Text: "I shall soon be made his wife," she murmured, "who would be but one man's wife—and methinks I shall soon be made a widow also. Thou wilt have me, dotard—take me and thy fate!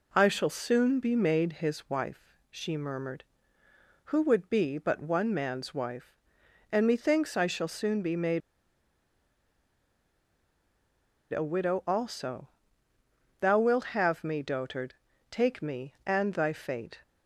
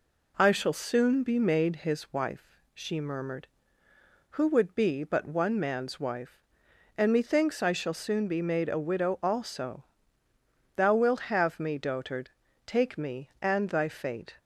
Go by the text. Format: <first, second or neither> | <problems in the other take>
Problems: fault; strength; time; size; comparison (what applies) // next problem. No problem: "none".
second | pauses between "made" and "a"; strong; at 8.4 s; 2.9 s long